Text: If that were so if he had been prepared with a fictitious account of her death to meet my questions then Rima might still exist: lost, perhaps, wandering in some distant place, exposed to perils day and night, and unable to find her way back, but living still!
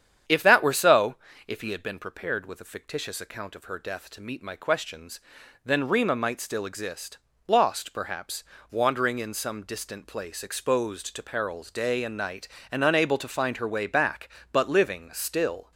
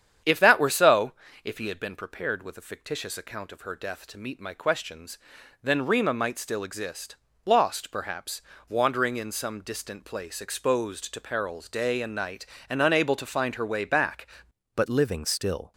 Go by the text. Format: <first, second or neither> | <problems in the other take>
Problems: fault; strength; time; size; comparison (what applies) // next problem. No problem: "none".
first | starts louder than the rest; strong; until 1.5 s; 8.5 dB; strong in the first // pauses between "so" and "if"; slight; at 1.1 s; 0.30 s long; slight in the first // pauses between "questions" and "then"; noticeable; at 5.1 s; 0.46 s long; noticeable in the first // changes voice at "but"; from 14.7 s on; 1.0 s long